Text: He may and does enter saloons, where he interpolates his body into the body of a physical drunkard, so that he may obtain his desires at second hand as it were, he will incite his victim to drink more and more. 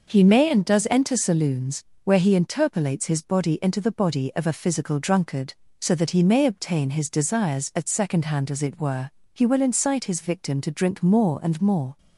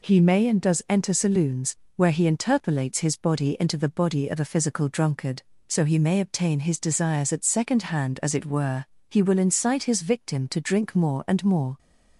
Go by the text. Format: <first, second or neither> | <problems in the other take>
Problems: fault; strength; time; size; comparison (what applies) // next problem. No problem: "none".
first | skips "that"; at 5.8 s